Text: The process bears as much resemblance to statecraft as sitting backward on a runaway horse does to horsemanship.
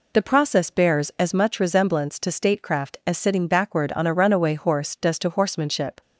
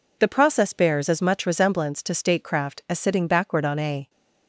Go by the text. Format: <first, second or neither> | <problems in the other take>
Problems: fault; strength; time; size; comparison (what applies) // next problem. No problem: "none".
first | stops before "runaway horse does to horsemanship"; at 4.0 s